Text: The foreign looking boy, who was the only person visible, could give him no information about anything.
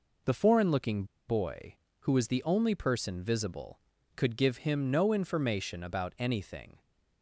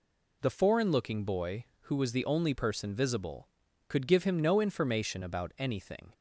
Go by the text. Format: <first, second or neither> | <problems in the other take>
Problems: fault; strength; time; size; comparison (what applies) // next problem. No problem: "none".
second | pauses between "looking" and "boy"; slight; at 1.0 s; 0.24 s long